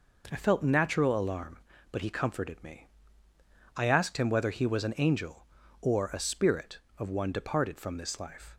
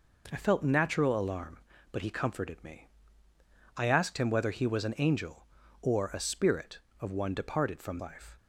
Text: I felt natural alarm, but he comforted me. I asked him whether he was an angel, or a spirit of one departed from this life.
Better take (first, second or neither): first